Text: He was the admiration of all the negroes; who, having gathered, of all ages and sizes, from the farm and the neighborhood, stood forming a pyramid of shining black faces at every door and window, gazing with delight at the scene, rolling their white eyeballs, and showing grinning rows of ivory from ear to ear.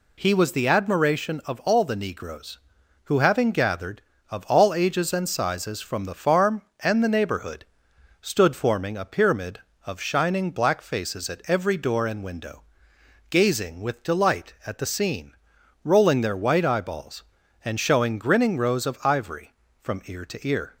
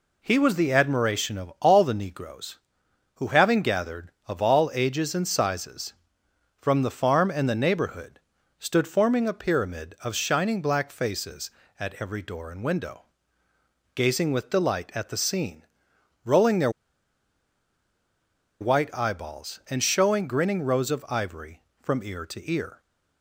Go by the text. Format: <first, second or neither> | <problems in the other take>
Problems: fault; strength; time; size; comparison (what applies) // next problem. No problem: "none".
first | pauses between "their" and "white"; strong; at 16.6 s; 1.9 s long